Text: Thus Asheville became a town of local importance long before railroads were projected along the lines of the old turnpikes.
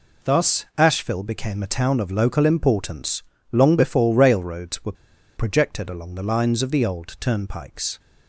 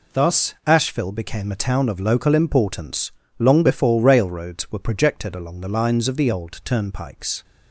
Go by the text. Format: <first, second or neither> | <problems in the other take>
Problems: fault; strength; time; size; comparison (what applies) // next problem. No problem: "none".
second | pauses between "importance" and "long"; slight; at 3.2 s; 0.28 s long; slight in the second // pauses between "were" and "projected"; at 4.9 s; 0.43 s long